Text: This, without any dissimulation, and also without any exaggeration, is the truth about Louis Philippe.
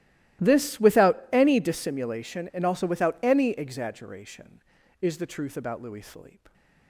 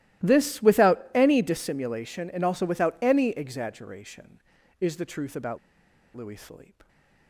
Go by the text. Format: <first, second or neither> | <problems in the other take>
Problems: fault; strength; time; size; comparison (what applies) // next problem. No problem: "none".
first | starts louder than the rest; strong; until 1.3 s; 15.5 dB; strong in the first // pauses between "about" and "Louis"; noticeable; at 5.5 s; 0.57 s long